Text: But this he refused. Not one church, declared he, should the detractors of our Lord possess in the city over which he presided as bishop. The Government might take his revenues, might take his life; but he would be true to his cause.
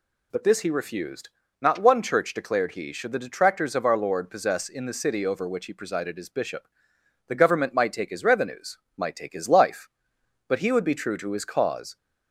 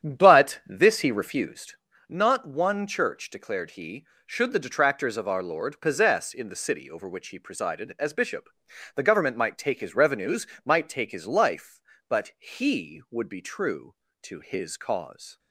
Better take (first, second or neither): first